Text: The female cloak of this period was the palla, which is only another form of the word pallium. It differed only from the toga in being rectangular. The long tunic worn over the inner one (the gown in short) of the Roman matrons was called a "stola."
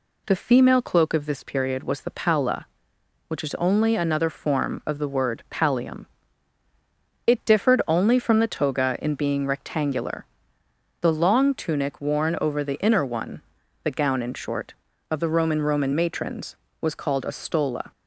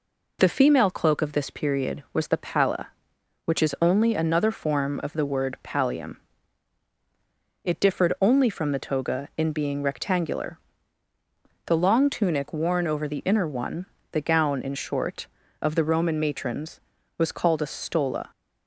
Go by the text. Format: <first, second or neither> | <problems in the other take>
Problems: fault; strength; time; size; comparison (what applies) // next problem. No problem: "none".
second | says "Roman" twice; at 15.5 s